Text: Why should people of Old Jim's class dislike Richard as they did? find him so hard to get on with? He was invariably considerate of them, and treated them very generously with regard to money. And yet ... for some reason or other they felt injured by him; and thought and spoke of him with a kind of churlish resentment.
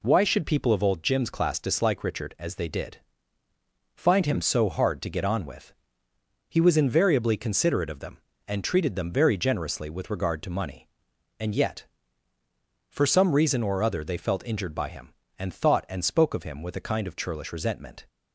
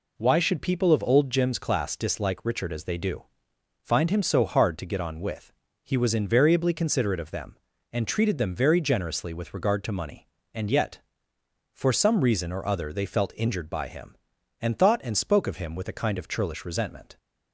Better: first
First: none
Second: says "do" for "did"; at 2.9 s

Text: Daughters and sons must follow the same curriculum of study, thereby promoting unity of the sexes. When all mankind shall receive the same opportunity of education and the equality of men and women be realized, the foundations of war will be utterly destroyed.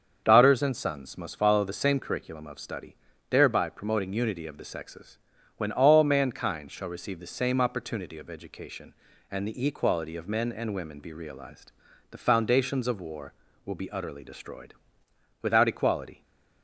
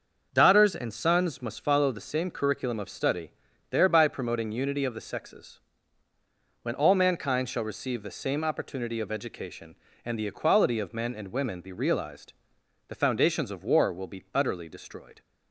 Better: second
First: starts louder than the rest; until 1.2 s; 6.5 dB // goes on to say "Without equality"; noticeable; from 15.4 s on; 0.80 s long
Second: starts louder than the rest; until 1.3 s; 6.5 dB

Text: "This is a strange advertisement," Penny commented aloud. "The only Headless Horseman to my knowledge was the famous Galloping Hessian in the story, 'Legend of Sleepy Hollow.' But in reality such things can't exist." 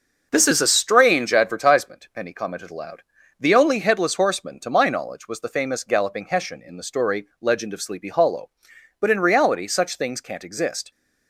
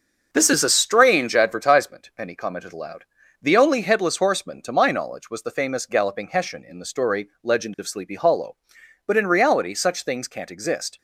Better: neither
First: starts louder than the rest; until 1.3 s; 6.5 dB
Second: starts louder than the rest; until 1.3 s; 6.5 dB

